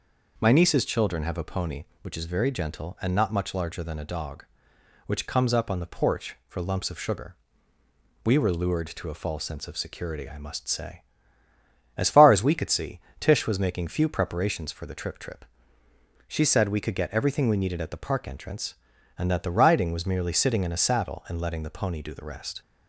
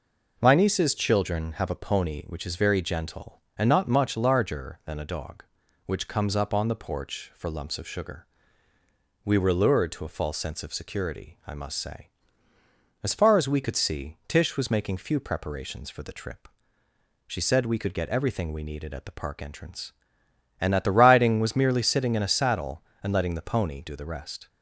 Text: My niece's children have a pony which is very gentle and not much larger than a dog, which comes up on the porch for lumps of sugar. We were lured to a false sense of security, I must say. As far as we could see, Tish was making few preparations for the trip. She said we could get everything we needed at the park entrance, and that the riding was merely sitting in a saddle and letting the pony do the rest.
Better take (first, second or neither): second